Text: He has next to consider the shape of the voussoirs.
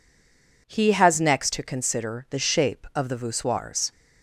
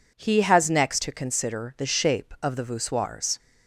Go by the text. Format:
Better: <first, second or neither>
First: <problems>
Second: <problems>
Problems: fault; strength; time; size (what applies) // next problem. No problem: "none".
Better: second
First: stays silent before the first word; slight; until 0.6 s; 0.6 s long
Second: none